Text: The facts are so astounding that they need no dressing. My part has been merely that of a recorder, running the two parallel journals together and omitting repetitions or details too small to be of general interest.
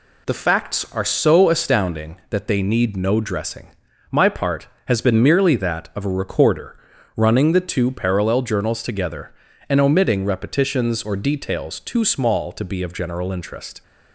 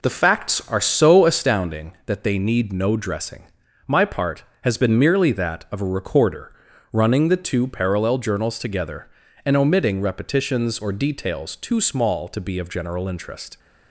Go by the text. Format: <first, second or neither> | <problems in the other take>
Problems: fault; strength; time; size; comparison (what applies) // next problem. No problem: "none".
first | starts louder than the rest; noticeable; until 1.5 s; 4 dB